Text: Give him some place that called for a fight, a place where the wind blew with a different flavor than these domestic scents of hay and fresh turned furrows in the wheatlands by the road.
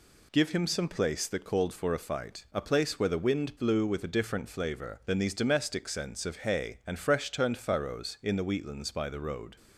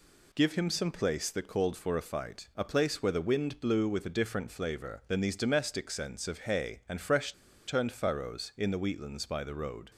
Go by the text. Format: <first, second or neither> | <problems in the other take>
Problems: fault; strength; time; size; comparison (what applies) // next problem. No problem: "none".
first | pauses between "fresh" and "turned"; slight; at 7.3 s; 0.33 s long